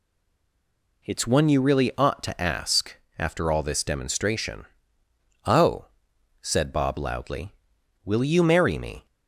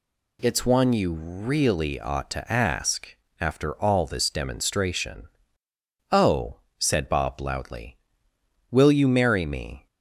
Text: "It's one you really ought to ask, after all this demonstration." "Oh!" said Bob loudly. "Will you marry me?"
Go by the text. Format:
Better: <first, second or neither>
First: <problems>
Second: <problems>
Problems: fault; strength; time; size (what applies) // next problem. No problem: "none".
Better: second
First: stays silent before the first word; until 1.0 s; 1.0 s long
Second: none